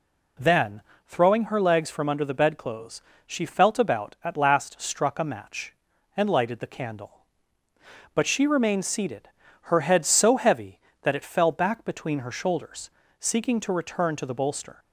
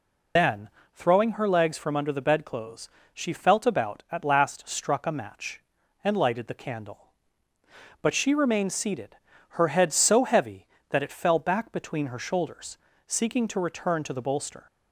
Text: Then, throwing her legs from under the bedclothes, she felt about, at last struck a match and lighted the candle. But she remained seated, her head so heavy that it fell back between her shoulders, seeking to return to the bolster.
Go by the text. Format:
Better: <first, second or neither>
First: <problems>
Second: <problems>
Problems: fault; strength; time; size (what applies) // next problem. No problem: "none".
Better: first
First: none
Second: loses the start of "Then"; at 0.3 s; 90 ms